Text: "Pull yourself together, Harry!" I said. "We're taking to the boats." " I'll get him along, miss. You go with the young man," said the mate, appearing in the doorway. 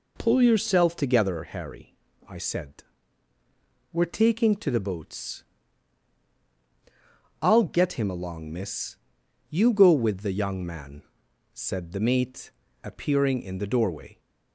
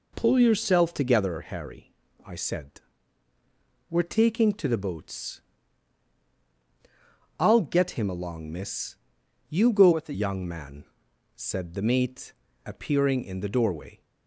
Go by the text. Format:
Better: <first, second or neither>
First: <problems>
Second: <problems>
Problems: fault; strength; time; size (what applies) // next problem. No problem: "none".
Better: first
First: none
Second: changes voice from "with" to "the"; from 9.9 to 10.1 s; 0.2 s long